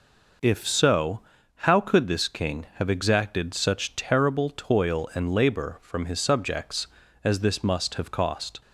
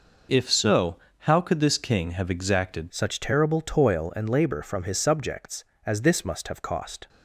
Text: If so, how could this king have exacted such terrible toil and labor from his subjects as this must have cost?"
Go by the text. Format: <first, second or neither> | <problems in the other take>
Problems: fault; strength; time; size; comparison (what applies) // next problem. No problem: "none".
first | changes voice at "such"; from 2.9 s on; 4.1 s long